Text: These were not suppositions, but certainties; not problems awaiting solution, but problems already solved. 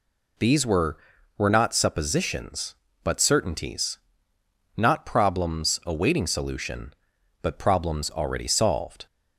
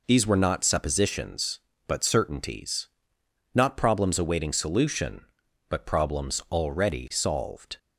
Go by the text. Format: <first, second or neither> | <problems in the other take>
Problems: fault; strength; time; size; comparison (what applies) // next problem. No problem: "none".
second | says "were" twice; at 1.3 s